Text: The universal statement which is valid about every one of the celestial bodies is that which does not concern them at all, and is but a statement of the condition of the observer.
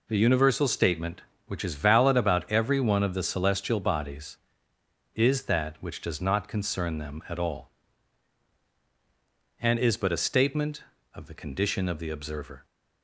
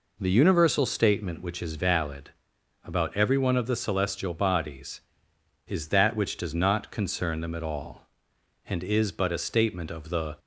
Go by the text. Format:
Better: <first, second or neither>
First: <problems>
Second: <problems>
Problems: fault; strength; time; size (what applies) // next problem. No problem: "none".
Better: first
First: none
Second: pauses between "valid" and "about"; noticeable; at 2.3 s; 0.52 s long // stops before "condition of the observer"; at 10.3 s